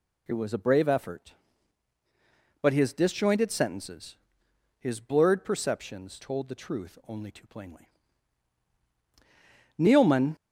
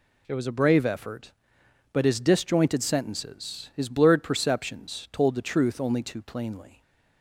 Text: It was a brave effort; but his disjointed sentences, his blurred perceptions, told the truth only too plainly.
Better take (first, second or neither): second